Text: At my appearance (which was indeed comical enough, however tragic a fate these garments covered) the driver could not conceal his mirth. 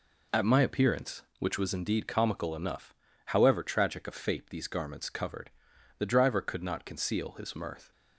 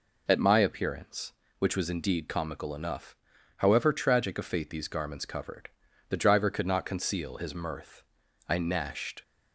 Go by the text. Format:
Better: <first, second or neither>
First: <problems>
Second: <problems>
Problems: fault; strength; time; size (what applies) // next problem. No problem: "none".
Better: first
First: none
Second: goes on to say "I gnashed"; noticeable; from 8.4 s on; 0.74 s long